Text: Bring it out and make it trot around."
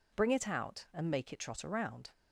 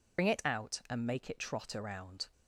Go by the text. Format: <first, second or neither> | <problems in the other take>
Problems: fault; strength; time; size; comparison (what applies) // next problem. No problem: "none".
first | loses the start of "Bring"; at 0.1 s; 70 ms